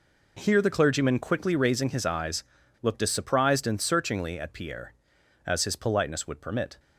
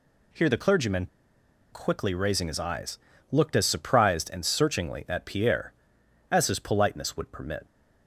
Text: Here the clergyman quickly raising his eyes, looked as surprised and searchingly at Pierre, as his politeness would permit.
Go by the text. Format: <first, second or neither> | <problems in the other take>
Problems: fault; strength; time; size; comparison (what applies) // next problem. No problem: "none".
first | pauses between "clergyman" and "quickly"; noticeable; at 1.0 s; 0.65 s long